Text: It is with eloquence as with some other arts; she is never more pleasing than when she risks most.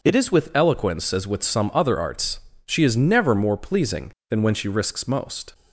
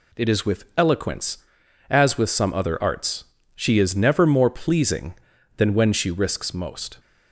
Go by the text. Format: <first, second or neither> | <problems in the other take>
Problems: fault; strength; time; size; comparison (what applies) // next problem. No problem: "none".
neither | none